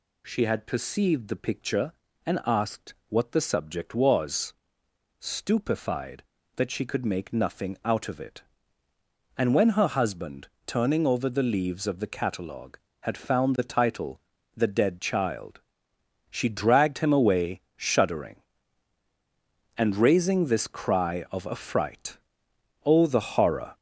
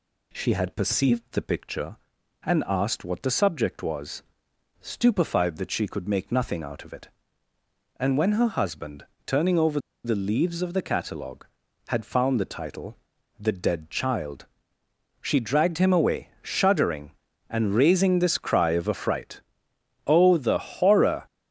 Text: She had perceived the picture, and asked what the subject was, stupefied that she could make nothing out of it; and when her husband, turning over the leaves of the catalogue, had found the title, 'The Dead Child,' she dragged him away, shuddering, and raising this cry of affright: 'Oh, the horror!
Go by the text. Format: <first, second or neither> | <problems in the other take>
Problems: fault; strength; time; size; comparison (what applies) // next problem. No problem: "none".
first | pauses between "over" and "the"; slight; at 9.7 s; 0.26 s long